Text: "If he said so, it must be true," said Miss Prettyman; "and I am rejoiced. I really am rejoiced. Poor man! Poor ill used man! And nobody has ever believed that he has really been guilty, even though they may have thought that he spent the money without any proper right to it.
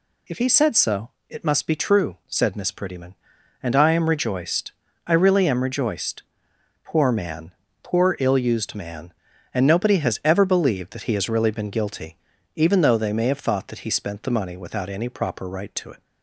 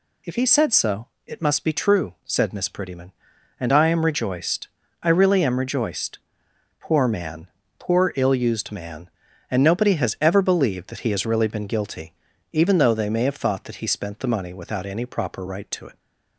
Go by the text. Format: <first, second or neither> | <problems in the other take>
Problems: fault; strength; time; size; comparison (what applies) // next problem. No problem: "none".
neither | none